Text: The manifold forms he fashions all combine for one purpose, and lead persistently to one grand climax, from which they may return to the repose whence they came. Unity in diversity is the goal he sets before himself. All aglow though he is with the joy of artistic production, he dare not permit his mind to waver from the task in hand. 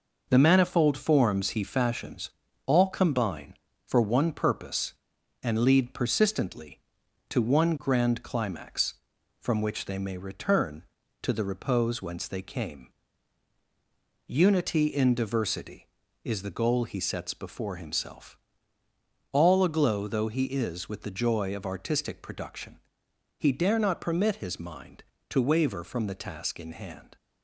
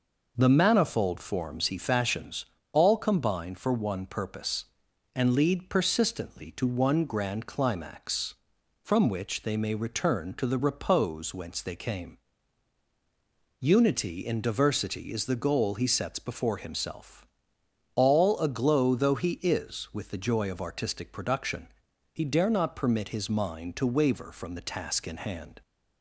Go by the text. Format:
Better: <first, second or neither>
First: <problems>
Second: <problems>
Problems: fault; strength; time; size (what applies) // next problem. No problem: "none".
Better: second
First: gets quieter; noticeable; throughout; 5.5 dB // pauses between "fashions" and "all"; slight; at 2.2 s; 0.36 s long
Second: pauses between "fashions" and "all"; slight; at 2.4 s; 0.28 s long